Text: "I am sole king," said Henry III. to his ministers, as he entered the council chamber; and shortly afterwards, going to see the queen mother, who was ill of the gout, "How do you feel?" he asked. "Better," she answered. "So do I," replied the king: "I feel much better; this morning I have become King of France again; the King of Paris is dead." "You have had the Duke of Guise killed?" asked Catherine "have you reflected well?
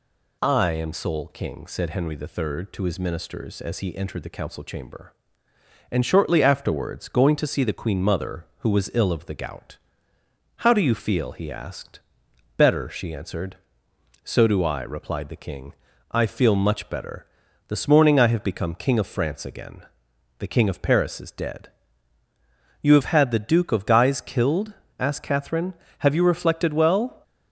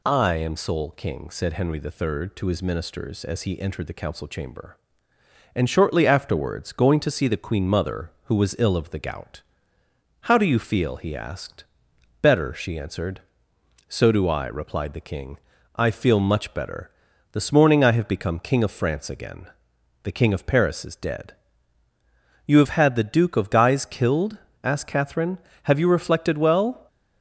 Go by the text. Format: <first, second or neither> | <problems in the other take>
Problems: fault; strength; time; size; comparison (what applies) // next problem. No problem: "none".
neither | none